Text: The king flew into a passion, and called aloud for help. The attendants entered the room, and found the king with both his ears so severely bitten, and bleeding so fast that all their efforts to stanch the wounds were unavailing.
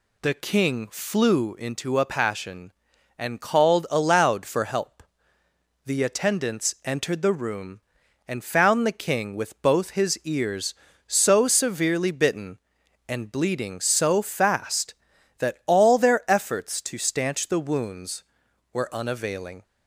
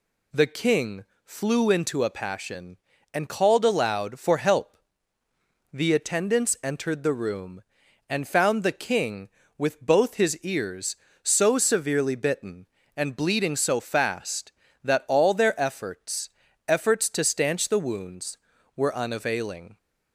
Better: first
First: none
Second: pauses between "king" and "flew"; slight; at 1.0 s; 0.22 s long // says "efforts" twice; at 16.6 s

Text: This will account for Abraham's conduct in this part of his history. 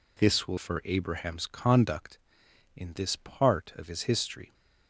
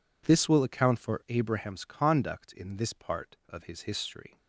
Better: second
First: skips "account"; at 0.5 s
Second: none

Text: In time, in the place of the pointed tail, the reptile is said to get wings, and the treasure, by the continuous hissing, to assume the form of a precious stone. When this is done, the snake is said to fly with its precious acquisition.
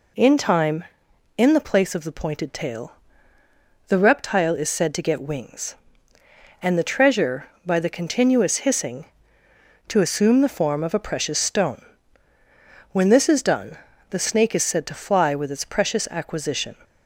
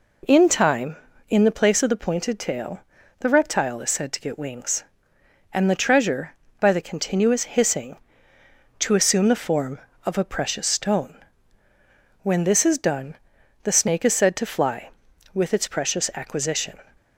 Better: neither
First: none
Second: none

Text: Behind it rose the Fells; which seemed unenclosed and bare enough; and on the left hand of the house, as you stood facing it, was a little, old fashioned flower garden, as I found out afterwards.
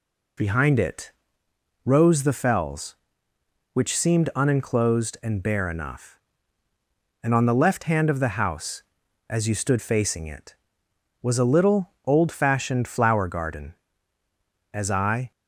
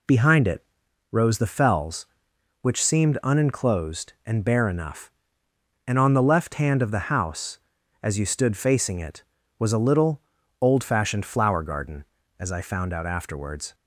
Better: second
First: pauses between "it" and "rose"; noticeable; at 1.1 s; 0.72 s long // stops before "found out afterwards"; at 15.3 s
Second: pauses between "it" and "rose"; noticeable; at 0.6 s; 0.46 s long

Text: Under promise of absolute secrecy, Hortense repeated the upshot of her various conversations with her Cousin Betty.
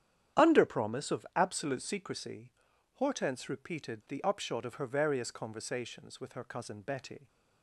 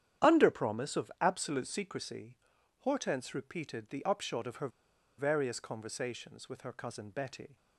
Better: first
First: starts louder than the rest; strong; until 1.4 s; 10 dB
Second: starts louder than the rest; strong; until 1.3 s; 10 dB // pauses between "her" and "various"; noticeable; at 4.6 s; 0.49 s long

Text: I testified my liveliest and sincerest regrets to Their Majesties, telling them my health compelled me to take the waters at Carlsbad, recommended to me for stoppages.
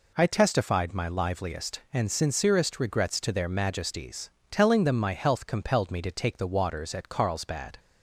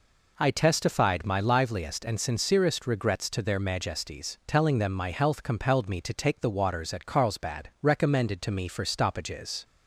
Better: second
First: stops before "recommended to me for stoppages"; at 7.7 s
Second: none

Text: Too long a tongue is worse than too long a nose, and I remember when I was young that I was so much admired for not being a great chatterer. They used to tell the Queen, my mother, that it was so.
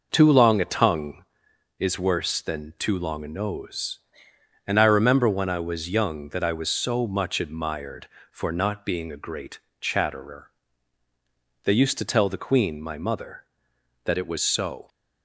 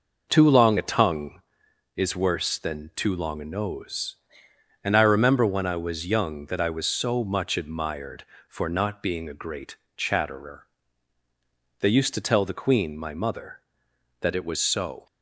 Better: neither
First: pauses between "great" and "chatterer"; slight; at 9.5 s; 0.20 s long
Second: pauses between "great" and "chatterer"; slight; at 9.7 s; 0.19 s long

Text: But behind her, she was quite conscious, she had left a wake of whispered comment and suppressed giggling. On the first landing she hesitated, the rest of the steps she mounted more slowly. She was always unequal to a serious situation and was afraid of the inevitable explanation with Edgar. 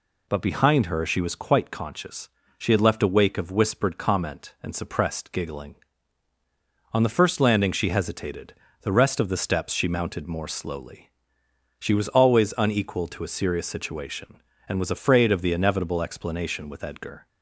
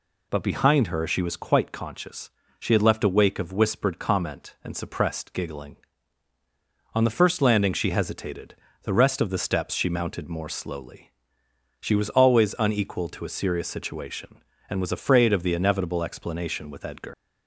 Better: first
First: none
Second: leaves "Edgar" unfinished; at 17.1 s; 145 ms

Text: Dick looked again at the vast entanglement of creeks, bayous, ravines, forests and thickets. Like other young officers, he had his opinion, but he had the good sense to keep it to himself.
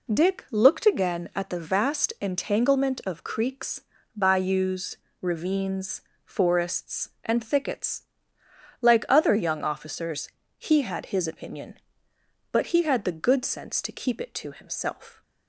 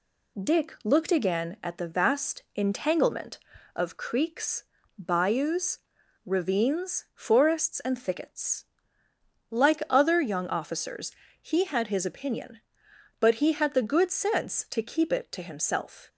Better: neither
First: none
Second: none

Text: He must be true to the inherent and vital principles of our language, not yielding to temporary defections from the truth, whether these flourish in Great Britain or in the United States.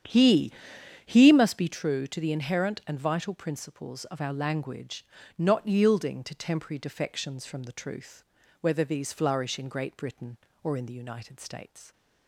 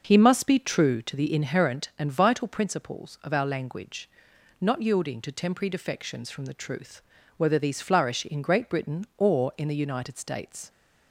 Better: second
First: starts louder than the rest; strong; until 1.6 s; 9 dB // says "He" twice; at 1.0 s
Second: starts louder than the rest; noticeable; until 1.0 s; 6 dB

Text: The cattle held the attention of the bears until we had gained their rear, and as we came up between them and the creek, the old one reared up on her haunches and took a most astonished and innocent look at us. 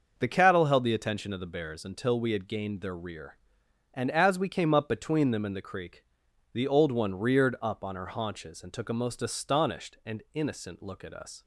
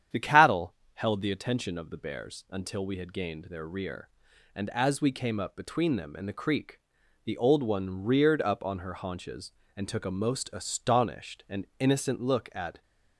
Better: first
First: starts louder than the rest; noticeable; until 1.1 s; 6 dB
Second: starts louder than the rest; strong; until 1.3 s; 9 dB // pauses between "cattle" and "held"; slight; at 0.7 s; 0.20 s long // stops before "us"; at 12.8 s

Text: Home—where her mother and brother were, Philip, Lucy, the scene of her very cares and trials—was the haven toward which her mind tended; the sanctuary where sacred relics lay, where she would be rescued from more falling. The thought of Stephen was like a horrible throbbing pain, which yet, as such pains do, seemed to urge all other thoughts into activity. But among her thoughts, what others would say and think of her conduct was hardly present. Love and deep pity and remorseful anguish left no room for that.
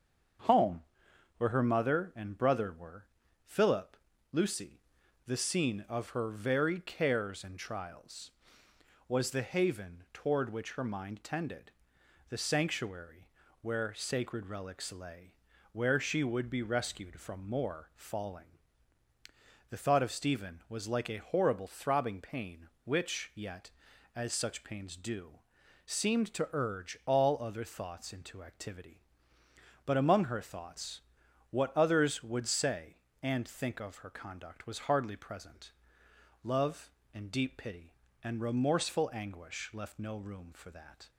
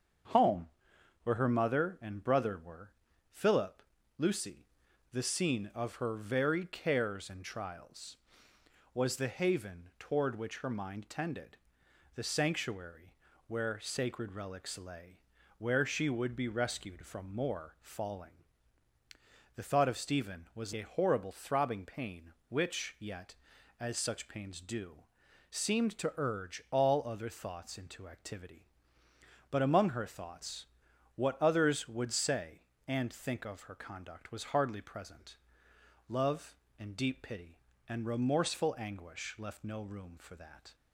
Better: first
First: starts louder than the rest; strong; until 2.0 s; 7 dB // pauses between "sanctuary" and "where"; slight; at 13.2 s; 0.34 s long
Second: starts louder than the rest; strong; until 1.8 s; 7 dB // pauses between "sanctuary" and "where"; slight; at 13.1 s; 0.34 s long // skips "like"; at 20.7 s

